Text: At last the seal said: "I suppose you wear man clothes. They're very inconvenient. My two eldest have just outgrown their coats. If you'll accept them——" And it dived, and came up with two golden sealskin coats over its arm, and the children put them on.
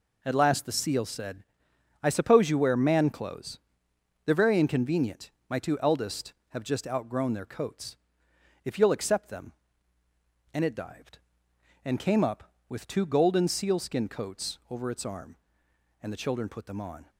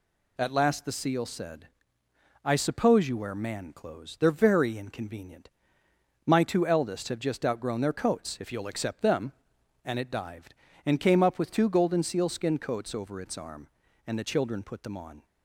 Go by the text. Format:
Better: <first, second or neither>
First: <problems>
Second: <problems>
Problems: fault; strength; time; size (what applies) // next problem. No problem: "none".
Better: neither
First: none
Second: none